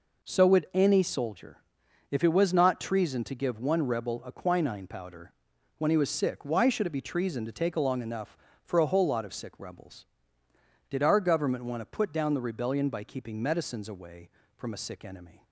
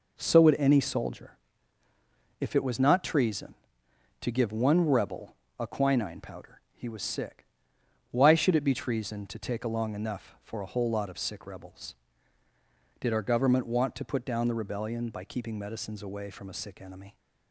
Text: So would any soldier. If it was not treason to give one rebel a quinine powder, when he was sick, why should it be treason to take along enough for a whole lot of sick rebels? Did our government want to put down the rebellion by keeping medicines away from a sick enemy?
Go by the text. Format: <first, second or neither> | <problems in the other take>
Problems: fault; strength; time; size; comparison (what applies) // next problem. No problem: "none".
first | pauses between "rebel" and "a"; slight; at 5.3 s; 0.24 s long // skips "when"; at 6.6 s